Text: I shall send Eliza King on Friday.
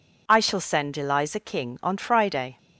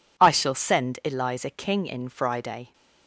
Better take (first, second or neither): first